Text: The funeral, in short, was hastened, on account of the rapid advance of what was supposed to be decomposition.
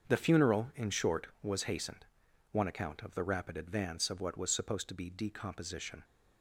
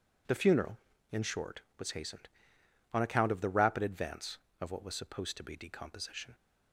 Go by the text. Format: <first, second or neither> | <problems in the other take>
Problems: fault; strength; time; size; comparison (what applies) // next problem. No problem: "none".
second | starts louder than the rest; until 1.1 s; 7 dB // says "one" for "on"; at 2.5 s